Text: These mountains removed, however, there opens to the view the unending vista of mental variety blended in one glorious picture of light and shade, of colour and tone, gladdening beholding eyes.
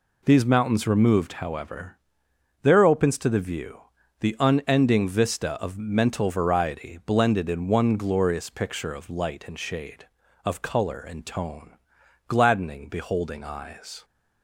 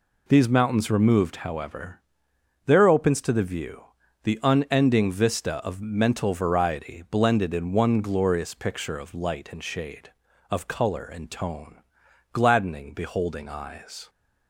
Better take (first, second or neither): neither